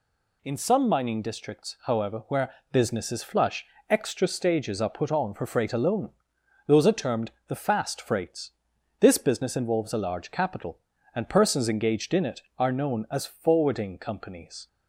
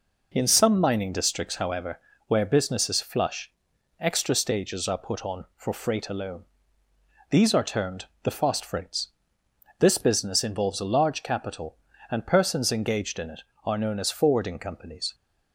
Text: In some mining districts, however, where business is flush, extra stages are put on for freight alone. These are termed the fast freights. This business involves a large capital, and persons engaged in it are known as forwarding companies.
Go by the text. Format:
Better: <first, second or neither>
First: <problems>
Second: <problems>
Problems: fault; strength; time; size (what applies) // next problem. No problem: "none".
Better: second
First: pauses between "where" and "business"; slight; at 2.5 s; 0.18 s long // says "Those" for "These"; at 6.6 s // pauses between "termed" and "the"; slight; at 7.3 s; 0.16 s long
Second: pauses between "termed" and "the"; slight; at 8.0 s; 0.16 s long